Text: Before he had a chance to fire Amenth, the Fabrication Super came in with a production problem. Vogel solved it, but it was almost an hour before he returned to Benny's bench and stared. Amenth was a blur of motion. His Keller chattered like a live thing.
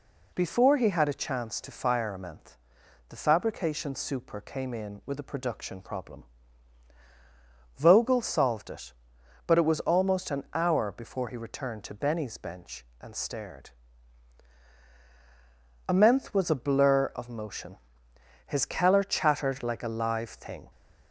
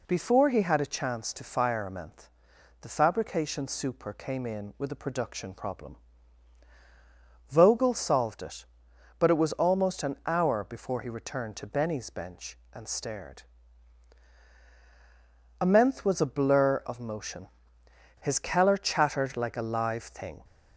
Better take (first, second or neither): neither